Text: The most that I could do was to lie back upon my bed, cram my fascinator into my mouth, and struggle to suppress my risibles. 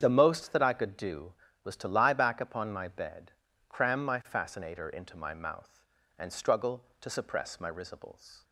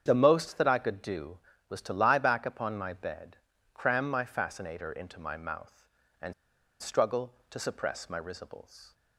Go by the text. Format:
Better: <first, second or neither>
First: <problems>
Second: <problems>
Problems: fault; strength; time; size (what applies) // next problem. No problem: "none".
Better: first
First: starts louder than the rest; strong; until 1.0 s; 8 dB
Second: starts louder than the rest; strong; until 1.0 s; 8 dB // pauses between "and" and "struggle"; noticeable; at 6.3 s; 0.47 s long